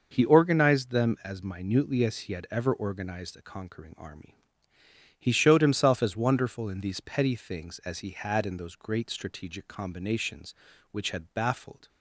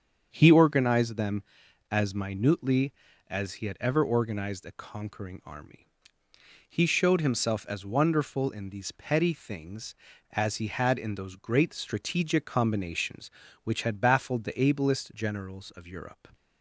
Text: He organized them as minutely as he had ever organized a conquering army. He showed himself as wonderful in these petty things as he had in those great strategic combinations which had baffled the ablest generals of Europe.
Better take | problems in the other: second | starts louder than the rest; noticeable; until 1.1 s; 6 dB; strong in the second // stops before "the ablest generals of Europe"; at 11.8 s

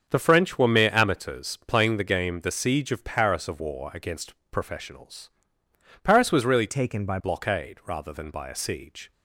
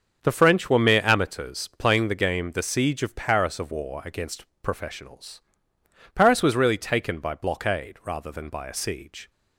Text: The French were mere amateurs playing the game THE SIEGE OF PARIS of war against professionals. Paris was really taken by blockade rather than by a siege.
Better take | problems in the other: second | starts louder than the rest; strong; until 1.1 s; 7.5 dB; strong in the second // pauses between "against" and "professionals"; slight; at 4.3 s; 0.18 s long; slight in the second // changes voice from "taken" to "by"; from 6.6 to 7.1 s; 0.5 s long

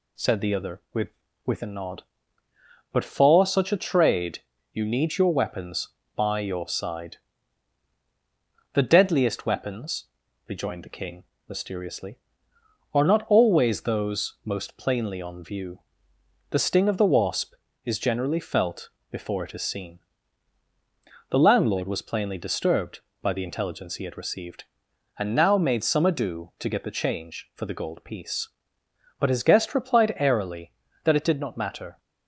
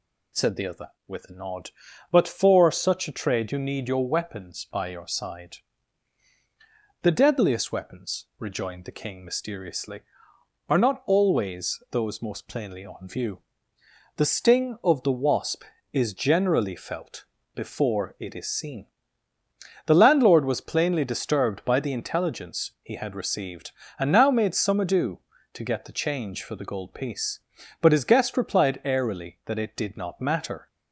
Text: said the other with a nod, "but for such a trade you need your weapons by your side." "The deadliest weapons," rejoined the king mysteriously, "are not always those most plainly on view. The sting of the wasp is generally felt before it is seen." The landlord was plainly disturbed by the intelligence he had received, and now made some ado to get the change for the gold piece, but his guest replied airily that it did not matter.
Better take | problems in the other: second | says "with" twice; at 1.4 s // pauses between "trade" and "you"; slight; at 4.4 s; 0.32 s long // pauses between "king" and "mysteriously"; slight; at 11.2 s; 0.22 s long // pauses between "felt" and "before"; slight; at 18.8 s; 0.22 s long; slight in the second

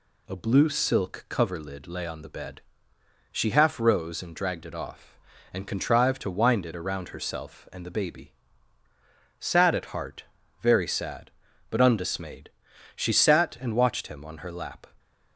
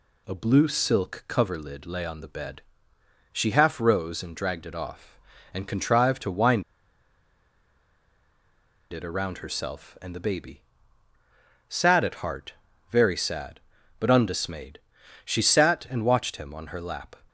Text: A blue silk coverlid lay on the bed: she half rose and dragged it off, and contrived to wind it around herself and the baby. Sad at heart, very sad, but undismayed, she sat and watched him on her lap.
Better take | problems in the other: first | pauses between "wind" and "it"; strong; at 6.6 s; 2.2 s long

